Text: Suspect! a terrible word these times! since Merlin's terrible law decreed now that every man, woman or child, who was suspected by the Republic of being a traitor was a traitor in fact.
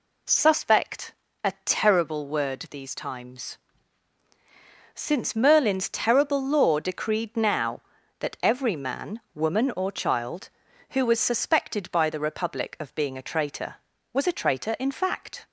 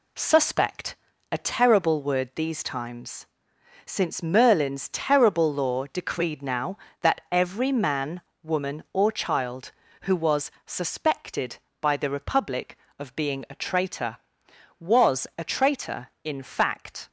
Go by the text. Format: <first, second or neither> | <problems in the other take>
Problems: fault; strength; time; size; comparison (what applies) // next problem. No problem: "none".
first | gets quieter; noticeable; throughout; 6 dB